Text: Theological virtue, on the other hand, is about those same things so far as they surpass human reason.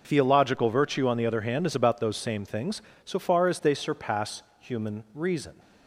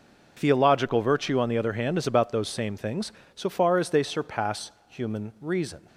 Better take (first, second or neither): neither